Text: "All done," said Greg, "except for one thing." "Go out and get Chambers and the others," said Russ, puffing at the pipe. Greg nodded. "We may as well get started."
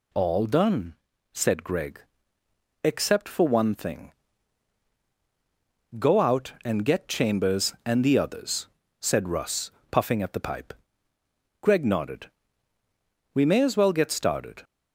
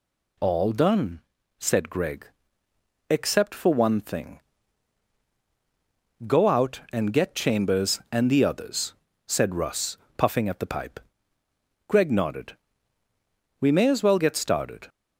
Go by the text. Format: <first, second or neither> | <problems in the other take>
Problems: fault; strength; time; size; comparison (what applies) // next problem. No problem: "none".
neither | none